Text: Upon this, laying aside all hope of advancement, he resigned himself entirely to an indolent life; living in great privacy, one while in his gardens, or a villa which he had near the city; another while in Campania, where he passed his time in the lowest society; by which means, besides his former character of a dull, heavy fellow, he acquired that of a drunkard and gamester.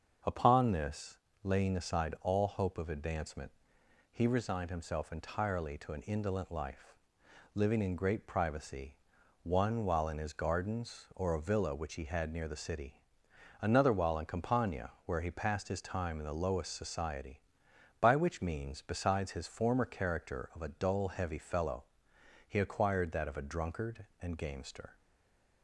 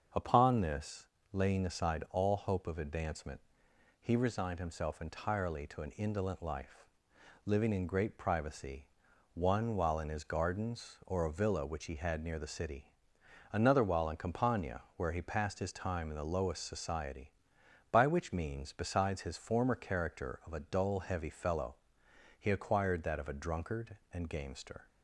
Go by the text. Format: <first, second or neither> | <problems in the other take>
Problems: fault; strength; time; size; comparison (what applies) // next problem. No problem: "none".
second | starts louder than the rest; until 1.5 s; 7 dB; also in the second // stays silent after the last word; slight; from 24.9 s on; 0.7 s long